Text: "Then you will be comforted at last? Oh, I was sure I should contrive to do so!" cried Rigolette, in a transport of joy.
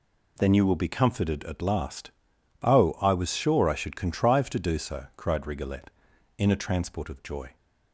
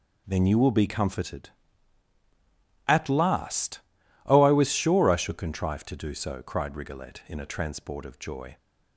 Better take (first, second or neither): neither